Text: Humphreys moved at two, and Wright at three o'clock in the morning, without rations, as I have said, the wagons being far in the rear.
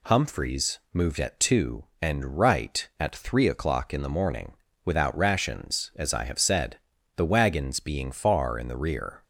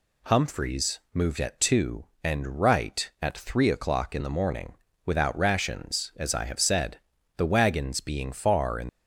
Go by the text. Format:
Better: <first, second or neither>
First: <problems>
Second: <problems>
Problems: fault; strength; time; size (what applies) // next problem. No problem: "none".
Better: first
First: none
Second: stops before "the rear"; at 8.8 s